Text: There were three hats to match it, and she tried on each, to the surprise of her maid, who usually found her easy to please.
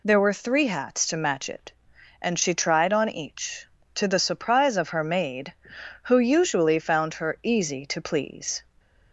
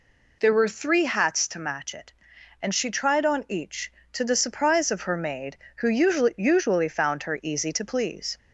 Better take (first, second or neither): first